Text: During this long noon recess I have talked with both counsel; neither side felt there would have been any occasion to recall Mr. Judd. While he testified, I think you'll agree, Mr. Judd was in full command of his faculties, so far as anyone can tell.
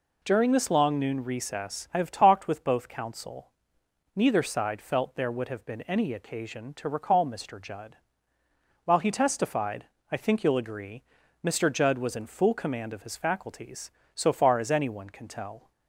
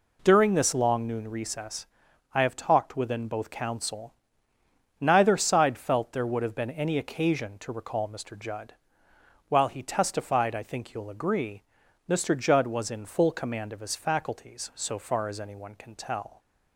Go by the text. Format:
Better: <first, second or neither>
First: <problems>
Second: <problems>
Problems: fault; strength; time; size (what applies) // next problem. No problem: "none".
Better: first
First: none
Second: pauses between "recess" and "I"; noticeable; at 1.8 s; 0.48 s long // says "within" for "with"; at 2.9 s